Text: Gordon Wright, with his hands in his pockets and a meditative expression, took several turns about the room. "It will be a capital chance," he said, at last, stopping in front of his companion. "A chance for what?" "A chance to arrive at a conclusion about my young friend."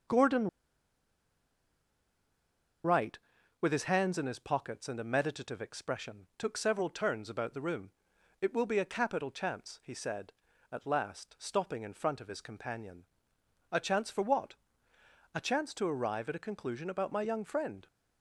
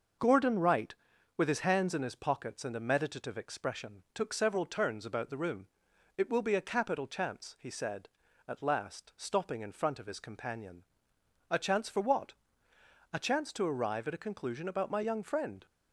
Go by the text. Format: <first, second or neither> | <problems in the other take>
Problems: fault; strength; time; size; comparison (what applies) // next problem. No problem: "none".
second | pauses between "Gordon" and "Wright"; strong; at 0.4 s; 2.3 s long